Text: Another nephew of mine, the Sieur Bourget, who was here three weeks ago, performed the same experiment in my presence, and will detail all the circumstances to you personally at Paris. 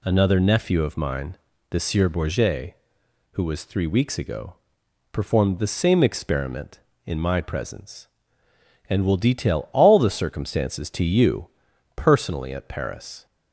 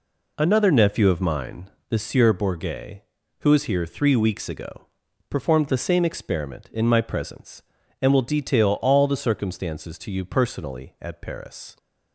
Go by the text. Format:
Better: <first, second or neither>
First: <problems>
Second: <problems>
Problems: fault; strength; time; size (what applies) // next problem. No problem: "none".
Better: second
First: skips "here"; at 3.6 s // pauses between "you" and "personally"; noticeable; at 11.4 s; 0.48 s long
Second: none